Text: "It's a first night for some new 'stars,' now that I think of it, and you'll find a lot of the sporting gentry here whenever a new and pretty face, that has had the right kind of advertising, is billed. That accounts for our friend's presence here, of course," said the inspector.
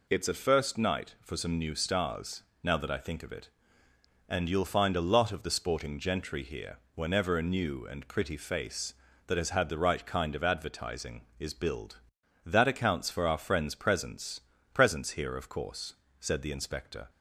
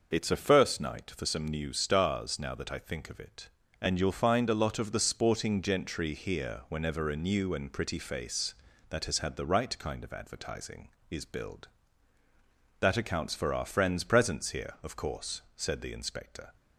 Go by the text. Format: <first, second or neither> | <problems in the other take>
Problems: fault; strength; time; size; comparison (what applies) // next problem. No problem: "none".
second | pauses between "here" and "whenever"; slight; at 6.7 s; 0.16 s long // says "presence" twice; at 14.7 s